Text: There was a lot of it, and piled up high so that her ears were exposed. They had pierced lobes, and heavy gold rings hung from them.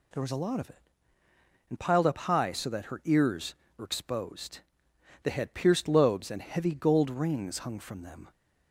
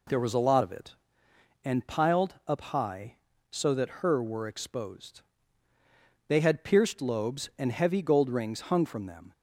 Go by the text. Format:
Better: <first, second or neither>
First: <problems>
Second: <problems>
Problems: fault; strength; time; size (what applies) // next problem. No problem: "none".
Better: first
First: none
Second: skips "ears"; at 4.2 s